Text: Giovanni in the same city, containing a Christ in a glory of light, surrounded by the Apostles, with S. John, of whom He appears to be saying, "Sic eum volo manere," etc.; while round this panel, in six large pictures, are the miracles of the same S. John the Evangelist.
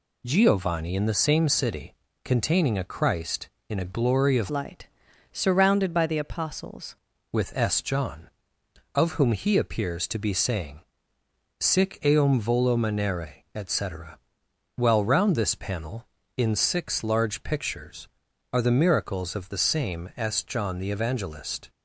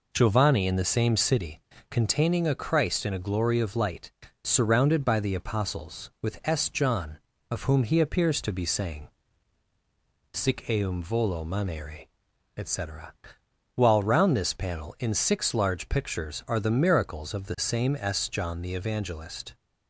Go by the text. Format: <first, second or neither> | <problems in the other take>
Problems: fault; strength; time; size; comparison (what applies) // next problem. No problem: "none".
second | changes voice from "light" to "Apostles"; from 4.5 to 6.9 s; 2.4 s long